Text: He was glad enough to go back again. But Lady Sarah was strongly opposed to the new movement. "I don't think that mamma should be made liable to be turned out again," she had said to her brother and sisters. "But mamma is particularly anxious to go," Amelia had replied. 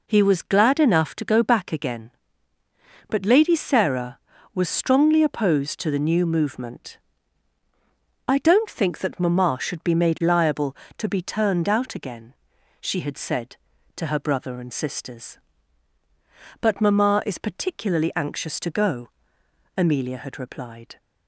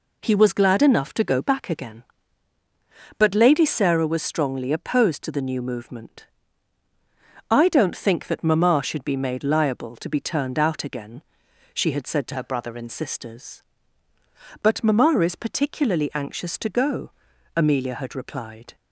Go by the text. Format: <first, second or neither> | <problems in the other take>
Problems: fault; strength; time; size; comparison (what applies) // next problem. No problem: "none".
first | changes voice from "her" to "and"; from 12.3 to 12.8 s; 0.5 s long